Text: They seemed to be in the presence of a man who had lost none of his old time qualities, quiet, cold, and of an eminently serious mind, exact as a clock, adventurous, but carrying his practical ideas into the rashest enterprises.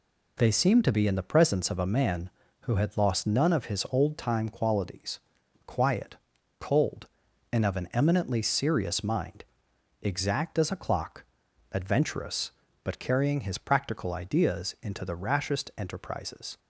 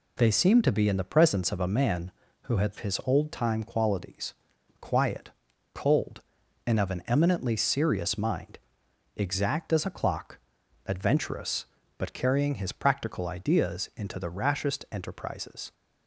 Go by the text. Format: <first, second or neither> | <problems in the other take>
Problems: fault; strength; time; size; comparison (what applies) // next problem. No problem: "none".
first | skips "lost none of"; at 2.7 s